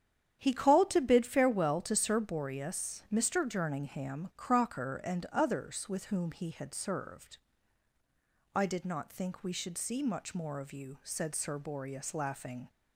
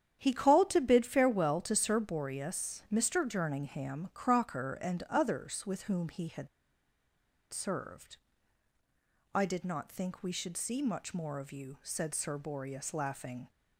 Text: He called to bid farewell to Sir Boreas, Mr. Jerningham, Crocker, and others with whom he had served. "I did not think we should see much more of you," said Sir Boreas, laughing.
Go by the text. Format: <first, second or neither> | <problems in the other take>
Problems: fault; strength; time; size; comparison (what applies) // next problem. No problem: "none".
first | starts louder than the rest; strong; until 1.2 s; 9.5 dB; strong in the first // pauses between "had" and "served"; at 6.4 s; 1.0 s long